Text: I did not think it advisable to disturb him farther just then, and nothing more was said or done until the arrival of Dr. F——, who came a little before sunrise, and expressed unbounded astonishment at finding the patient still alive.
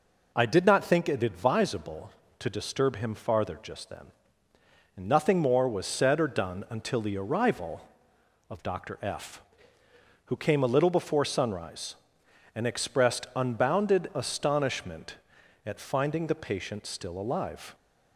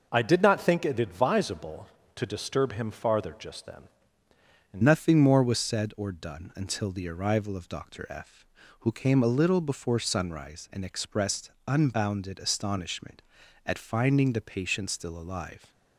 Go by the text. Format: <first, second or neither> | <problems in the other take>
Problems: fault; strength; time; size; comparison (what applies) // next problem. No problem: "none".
first | changes voice at "nothing"; from 4.8 s on; 10.9 s long // pauses between "expressed" and "unbounded"; slight; at 11.4 s; 0.16 s long